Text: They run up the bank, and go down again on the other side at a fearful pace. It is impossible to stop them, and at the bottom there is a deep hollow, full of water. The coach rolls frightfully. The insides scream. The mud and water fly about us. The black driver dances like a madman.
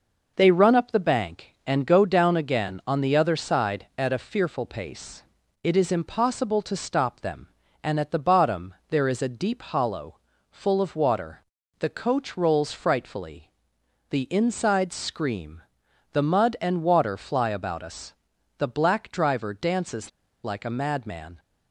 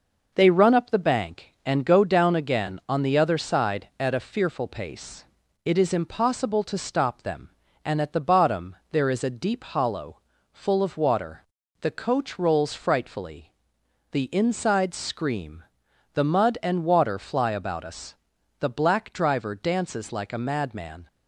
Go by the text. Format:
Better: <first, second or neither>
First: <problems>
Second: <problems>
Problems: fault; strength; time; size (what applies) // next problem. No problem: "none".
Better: second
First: pauses between "bottom" and "there"; slight; at 8.7 s; 0.16 s long // pauses between "dances" and "like"; slight; at 20.0 s; 0.34 s long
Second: pauses between "bottom" and "there"; slight; at 8.7 s; 0.16 s long